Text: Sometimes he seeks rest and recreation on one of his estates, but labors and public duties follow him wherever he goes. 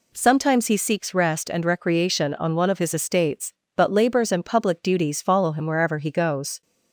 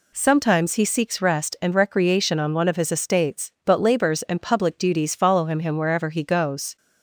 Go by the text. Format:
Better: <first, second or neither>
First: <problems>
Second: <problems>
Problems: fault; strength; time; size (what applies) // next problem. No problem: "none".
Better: first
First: none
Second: says "him" twice; at 5.6 s